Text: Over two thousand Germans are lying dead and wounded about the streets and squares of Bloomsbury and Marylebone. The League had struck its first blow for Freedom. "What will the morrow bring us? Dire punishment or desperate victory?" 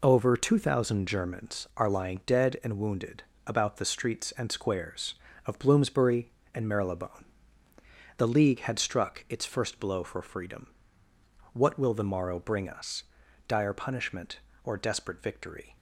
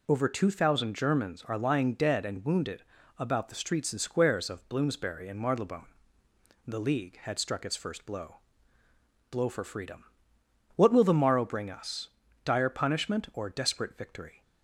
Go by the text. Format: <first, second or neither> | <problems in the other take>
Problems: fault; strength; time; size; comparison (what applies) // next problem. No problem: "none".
first | pauses between "wounded" and "about"; slight; at 2.8 s; 0.34 s long; slight in the first // says "blow" twice; at 9.2 s